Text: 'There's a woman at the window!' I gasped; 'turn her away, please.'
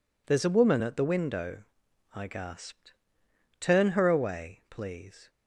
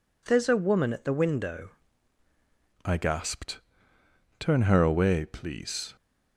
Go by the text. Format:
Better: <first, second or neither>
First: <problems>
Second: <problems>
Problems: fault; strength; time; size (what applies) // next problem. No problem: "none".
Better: first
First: none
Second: changes voice at "I"; from 2.8 s on; 3.1 s long